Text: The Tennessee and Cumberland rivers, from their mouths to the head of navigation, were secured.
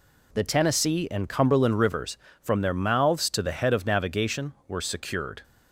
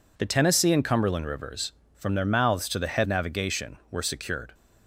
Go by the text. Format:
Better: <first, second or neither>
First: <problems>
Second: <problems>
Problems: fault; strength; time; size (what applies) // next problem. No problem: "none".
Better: first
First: none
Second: skips "of"; at 3.0 s